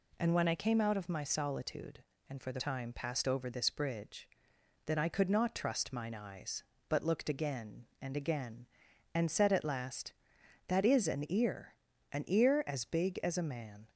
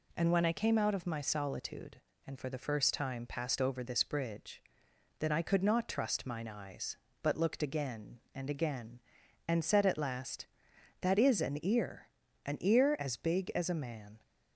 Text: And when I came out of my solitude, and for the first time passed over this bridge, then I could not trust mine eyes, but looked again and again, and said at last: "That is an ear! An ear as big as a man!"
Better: second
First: skips "first"; at 2.6 s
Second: none

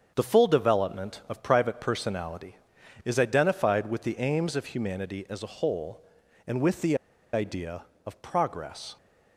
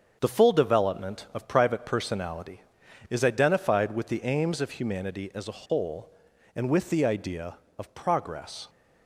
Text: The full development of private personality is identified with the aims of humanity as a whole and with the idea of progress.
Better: second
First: starts louder than the rest; until 1.1 s; 7 dB // pauses between "the" and "idea"; at 6.9 s; 0.38 s long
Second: starts louder than the rest; until 1.2 s; 6.5 dB

